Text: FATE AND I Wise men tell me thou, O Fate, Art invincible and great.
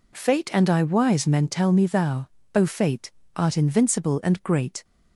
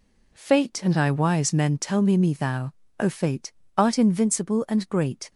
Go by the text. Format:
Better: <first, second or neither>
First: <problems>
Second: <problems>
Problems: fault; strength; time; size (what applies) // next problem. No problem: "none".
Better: first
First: none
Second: says "me" twice; at 2.1 s